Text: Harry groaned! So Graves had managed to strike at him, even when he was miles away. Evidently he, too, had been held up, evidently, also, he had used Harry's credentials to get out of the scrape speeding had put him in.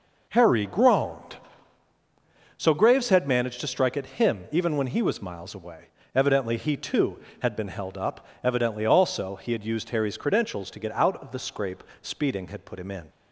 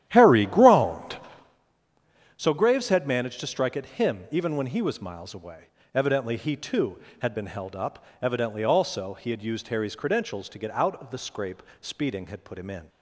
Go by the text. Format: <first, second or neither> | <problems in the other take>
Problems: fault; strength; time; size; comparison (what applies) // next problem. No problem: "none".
first | starts louder than the rest; strong; until 1.6 s; 11.5 dB // pauses between "scrape" and "speeding"; slight; at 11.6 s; 0.18 s long; slight in the first